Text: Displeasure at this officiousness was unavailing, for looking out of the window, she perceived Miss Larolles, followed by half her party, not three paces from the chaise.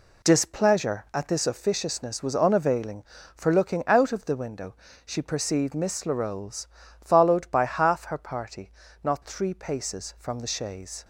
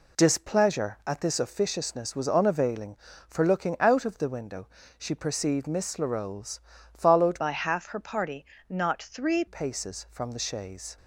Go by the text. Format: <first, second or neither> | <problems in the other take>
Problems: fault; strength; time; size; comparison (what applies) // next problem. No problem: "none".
first | changes voice from "by" to "three"; from 7.3 to 9.4 s; 2.1 s long